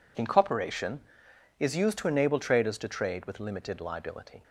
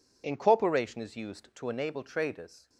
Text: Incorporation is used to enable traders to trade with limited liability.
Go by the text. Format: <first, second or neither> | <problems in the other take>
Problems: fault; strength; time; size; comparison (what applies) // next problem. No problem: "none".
first | stops before "to trade with limited liability"; at 2.6 s